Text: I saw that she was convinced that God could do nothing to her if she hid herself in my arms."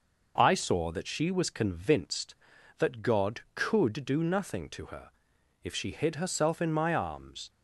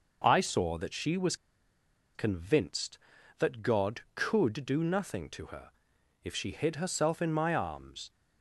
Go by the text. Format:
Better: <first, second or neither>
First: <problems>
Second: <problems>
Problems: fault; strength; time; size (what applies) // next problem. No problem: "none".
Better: first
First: pauses between "her" and "if"; noticeable; at 5.0 s; 0.54 s long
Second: pauses between "was" and "convinced"; noticeable; at 1.3 s; 0.80 s long // pauses between "her" and "if"; noticeable; at 5.6 s; 0.54 s long